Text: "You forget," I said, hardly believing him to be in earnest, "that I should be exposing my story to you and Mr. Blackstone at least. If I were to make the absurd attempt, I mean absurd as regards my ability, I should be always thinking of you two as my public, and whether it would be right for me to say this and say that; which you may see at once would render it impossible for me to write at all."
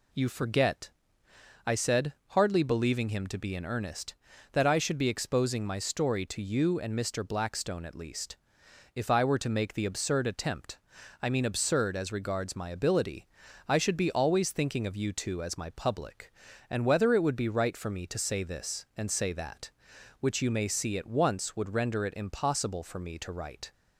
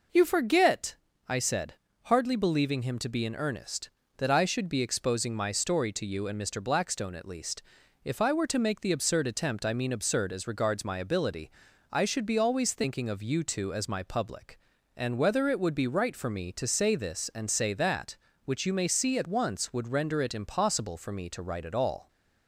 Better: second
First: stops before "at all"; at 23.7 s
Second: none

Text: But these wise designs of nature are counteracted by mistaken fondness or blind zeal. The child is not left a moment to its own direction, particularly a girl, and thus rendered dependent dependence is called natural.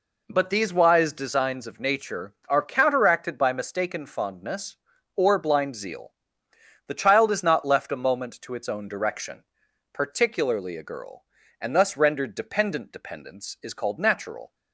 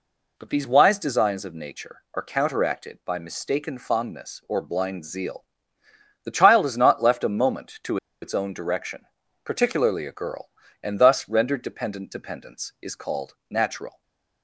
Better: first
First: none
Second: pauses between "to" and "its"; slight; at 7.9 s; 0.25 s long // stays silent after the last word; slight; from 13.8 s on; 0.6 s long

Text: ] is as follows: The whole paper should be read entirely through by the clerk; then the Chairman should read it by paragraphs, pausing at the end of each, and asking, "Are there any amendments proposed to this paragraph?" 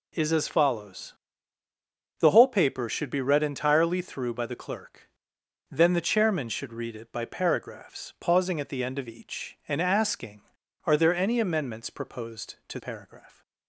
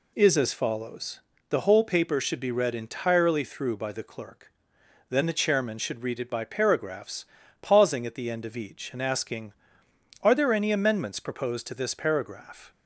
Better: second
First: skips "this"; at 12.7 s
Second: none

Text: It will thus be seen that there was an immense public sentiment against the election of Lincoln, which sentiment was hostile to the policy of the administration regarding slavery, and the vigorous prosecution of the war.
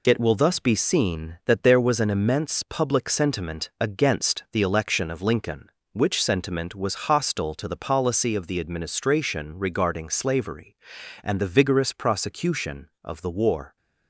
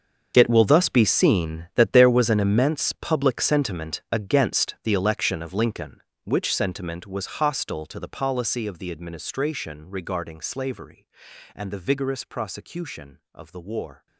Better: first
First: none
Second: gets quieter; strong; throughout; 16.5 dB

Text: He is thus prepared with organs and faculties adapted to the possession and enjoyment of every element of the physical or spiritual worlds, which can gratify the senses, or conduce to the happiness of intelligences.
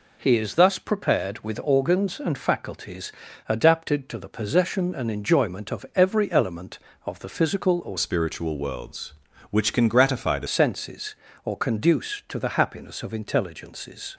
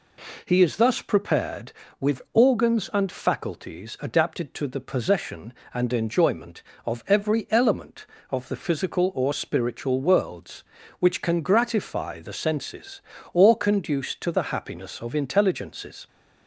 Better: second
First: pauses between "faculties" and "adapted"; slight; at 3.1 s; 0.34 s long // changes voice from "spiritual" to "the"; from 7.9 to 10.4 s; 2.5 s long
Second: none

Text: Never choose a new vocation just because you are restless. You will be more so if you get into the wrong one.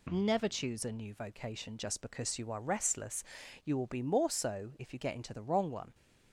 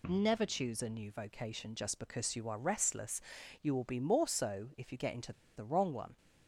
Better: first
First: none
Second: pauses between "into" and "the"; slight; at 5.3 s; 0.22 s long

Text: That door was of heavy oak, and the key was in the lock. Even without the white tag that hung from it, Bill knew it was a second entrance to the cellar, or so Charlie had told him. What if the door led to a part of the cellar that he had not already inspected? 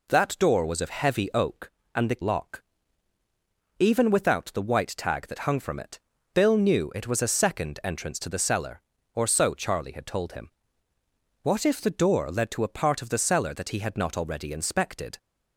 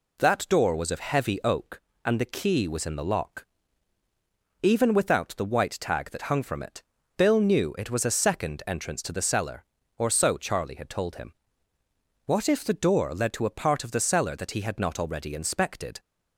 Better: second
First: skips "key was in the"; at 2.2 s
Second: none

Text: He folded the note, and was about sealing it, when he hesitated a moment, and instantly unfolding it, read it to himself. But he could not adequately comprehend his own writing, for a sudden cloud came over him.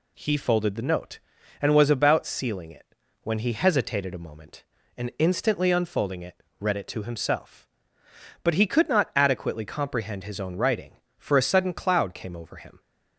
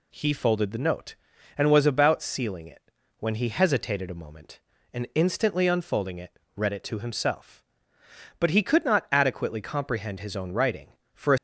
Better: first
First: none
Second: stops before "sudden cloud came over him"; at 11.3 s

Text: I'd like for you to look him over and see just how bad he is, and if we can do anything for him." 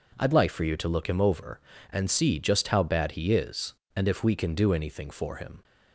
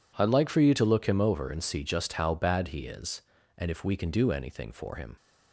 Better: neither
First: none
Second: none

